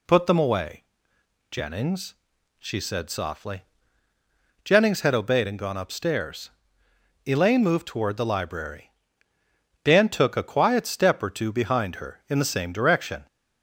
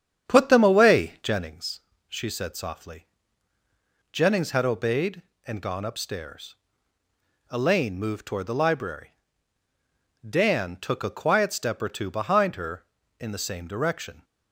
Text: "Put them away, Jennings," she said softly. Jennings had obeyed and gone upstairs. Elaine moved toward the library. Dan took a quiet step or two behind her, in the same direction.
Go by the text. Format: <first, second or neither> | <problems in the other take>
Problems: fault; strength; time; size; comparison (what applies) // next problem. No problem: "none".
first | starts louder than the rest; strong; until 1.5 s; 8.5 dB